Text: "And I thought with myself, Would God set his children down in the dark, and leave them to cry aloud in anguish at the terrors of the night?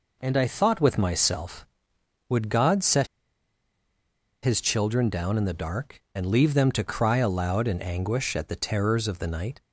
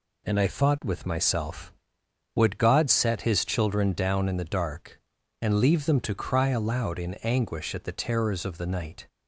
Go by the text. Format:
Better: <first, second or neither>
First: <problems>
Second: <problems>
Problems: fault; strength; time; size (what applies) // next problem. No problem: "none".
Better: second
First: pauses between "set" and "his"; strong; at 3.0 s; 1.3 s long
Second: none